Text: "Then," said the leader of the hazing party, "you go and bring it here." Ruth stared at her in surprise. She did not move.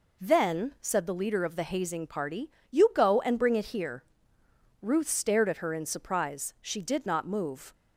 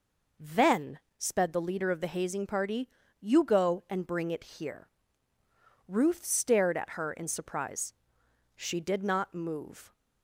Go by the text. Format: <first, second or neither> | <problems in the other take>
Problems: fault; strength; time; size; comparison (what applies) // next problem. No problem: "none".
first | says "sped" for "said"; at 1.1 s